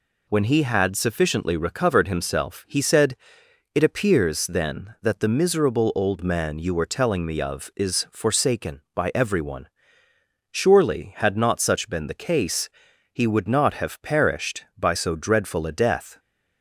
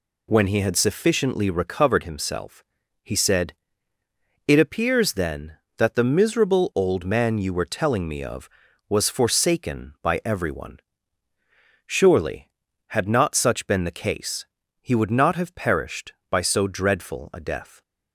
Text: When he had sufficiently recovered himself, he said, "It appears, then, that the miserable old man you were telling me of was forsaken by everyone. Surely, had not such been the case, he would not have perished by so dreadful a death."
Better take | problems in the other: second | says "is" for "was"; at 7.7 s

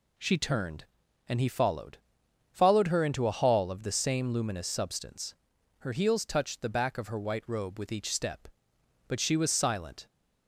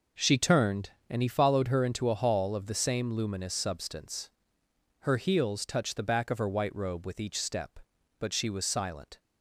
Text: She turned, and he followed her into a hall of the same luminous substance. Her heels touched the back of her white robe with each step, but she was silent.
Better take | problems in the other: second | says "followed" twice; at 2.5 s

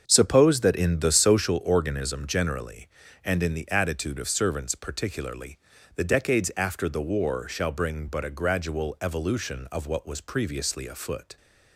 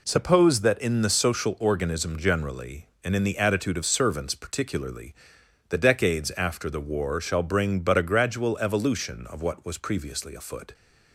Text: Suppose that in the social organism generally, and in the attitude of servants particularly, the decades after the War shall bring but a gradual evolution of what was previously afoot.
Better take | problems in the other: second | starts louder than the rest; until 1.6 s; 7 dB

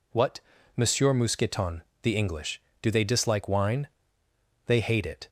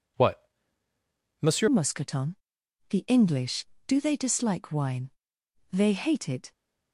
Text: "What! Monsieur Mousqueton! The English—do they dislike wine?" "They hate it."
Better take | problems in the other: first | changes voice at "Mousqueton"; from 1.6 s on; 4.9 s long

